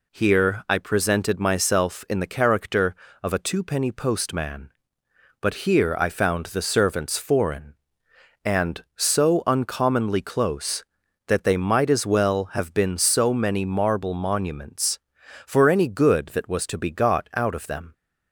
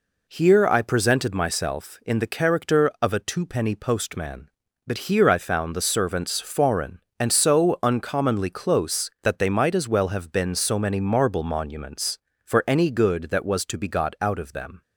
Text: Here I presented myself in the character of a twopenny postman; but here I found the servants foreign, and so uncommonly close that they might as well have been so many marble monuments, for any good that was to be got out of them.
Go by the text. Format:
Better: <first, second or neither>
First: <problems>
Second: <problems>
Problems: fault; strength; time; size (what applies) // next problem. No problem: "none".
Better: neither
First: none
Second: none